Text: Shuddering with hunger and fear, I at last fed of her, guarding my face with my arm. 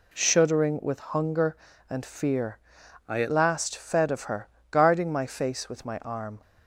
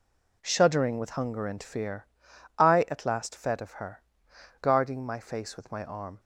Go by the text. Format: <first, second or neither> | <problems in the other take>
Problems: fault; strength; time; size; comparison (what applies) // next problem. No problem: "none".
second | changes voice from "I" to "at"; from 3.0 to 3.2 s; 0.2 s long